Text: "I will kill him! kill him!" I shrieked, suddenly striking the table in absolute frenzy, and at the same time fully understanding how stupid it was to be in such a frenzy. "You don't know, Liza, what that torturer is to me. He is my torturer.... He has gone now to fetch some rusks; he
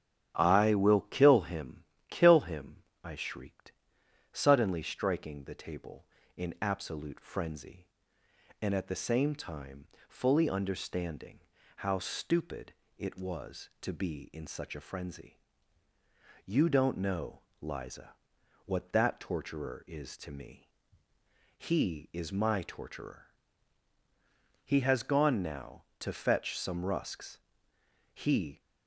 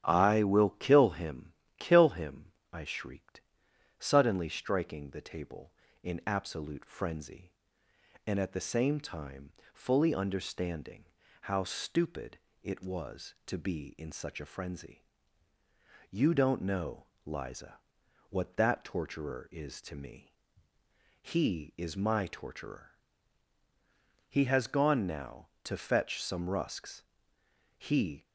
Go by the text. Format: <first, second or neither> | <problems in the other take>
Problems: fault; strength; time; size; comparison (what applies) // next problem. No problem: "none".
neither | starts louder than the rest; strong; the same in both // pauses between "time" and "fully"; slight; the same in both // pauses between "understanding" and "how"; the same in both // pauses between "stupid" and "it"; slight; the same in both